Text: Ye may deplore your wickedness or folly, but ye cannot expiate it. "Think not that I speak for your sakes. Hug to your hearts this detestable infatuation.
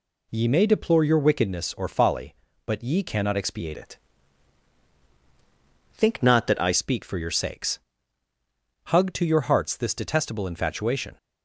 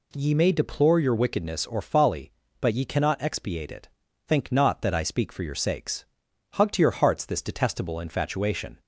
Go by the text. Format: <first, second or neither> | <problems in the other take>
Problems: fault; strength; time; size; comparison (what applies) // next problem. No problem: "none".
second | changes voice from "it" to "I"; from 3.7 to 6.7 s; 3.0 s long